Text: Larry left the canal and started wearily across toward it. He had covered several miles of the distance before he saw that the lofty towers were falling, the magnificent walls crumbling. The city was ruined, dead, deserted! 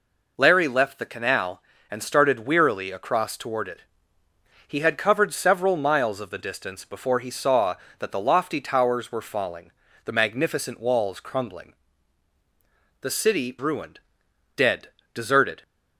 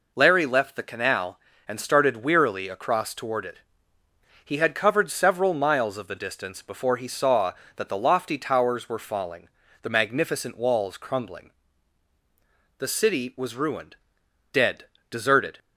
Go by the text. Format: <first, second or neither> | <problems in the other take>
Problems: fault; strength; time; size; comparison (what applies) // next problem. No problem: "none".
second | skips "was"; at 13.5 s